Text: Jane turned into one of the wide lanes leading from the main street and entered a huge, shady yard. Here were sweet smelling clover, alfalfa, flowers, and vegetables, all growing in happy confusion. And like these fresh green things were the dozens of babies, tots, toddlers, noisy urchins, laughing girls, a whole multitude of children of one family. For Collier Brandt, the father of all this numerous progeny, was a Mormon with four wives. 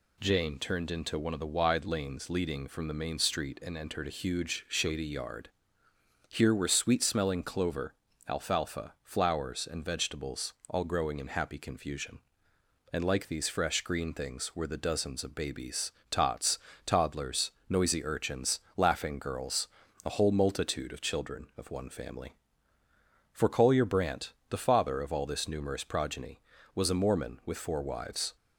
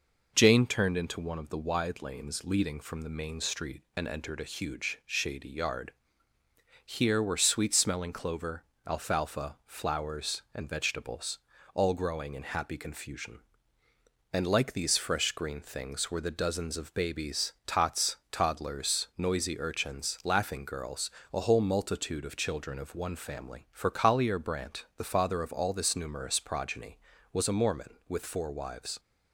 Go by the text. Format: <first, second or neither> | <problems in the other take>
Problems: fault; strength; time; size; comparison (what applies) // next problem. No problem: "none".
neither | none